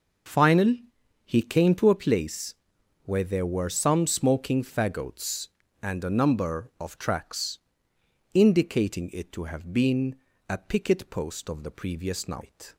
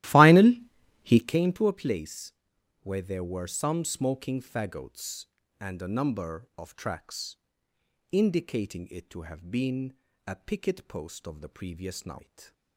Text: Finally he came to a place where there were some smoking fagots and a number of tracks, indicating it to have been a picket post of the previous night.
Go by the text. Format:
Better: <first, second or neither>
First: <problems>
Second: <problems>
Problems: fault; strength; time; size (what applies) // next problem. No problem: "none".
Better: first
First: pauses between "Finally" and "he"; at 0.8 s; 0.42 s long // pauses between "place" and "where"; noticeable; at 2.5 s; 0.52 s long // pauses between "been" and "a"; slight; at 10.1 s; 0.34 s long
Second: starts louder than the rest; strong; until 1.4 s; 15.5 dB // pauses between "Finally" and "he"; at 0.6 s; 0.42 s long // pauses between "place" and "where"; noticeable; at 2.3 s; 0.52 s long // pauses between "been" and "a"; slight; at 9.9 s; 0.34 s long